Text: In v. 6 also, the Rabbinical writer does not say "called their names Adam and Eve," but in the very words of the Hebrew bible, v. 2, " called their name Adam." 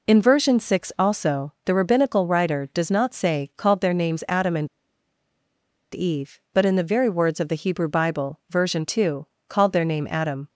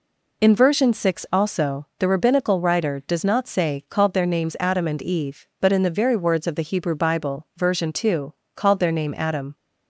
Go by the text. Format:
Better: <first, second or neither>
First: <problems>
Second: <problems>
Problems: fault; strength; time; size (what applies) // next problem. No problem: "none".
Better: second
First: pauses between "and" and "Eve"; at 4.6 s; 1.2 s long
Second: none